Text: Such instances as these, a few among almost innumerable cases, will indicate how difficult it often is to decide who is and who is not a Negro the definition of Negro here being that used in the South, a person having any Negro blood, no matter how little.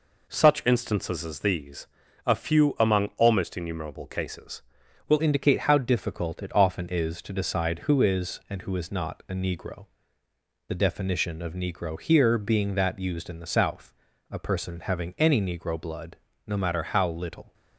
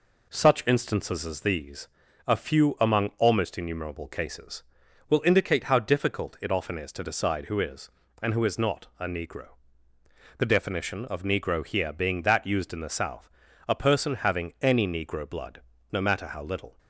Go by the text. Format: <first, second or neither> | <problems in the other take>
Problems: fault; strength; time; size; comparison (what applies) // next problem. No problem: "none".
second | changes voice at "indicate"; from 5.2 s on; 12.3 s long // pauses between "Negro" and "the"; noticeable; at 9.8 s; 0.82 s long; noticeable in the second